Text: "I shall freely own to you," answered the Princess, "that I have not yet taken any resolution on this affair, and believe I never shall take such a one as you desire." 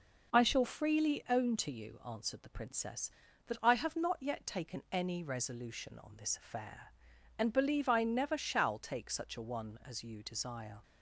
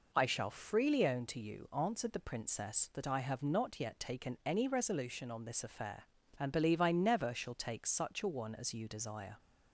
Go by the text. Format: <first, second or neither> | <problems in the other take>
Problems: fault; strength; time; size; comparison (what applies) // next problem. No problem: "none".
neither | none